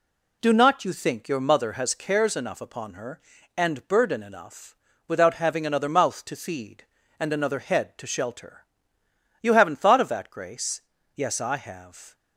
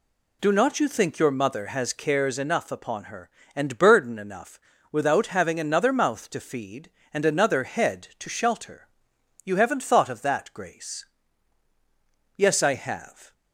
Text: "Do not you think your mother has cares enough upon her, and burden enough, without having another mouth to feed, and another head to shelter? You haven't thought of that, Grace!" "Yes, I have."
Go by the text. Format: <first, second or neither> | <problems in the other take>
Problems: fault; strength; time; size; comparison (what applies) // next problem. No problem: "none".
neither | none